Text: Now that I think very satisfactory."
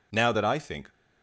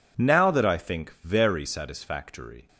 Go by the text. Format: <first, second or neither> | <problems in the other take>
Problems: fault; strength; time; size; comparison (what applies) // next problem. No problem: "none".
second | stops before "very satisfactory"; at 0.9 s